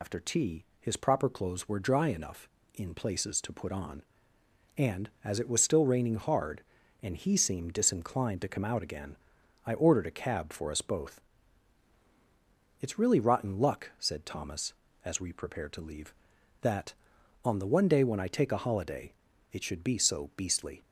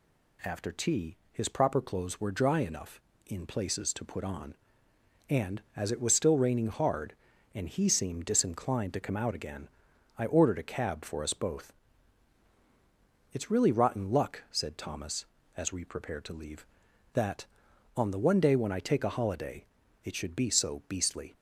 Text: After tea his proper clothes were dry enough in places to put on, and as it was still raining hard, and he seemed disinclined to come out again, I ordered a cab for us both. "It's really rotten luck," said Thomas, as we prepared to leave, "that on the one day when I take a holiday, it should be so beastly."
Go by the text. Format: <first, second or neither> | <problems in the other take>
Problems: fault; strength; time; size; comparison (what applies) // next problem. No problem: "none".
second | loses the start of "After"; at 0.0 s; 140 ms // pauses between "tea" and "his"; slight; at 0.6 s; 0.16 s long; slight in the second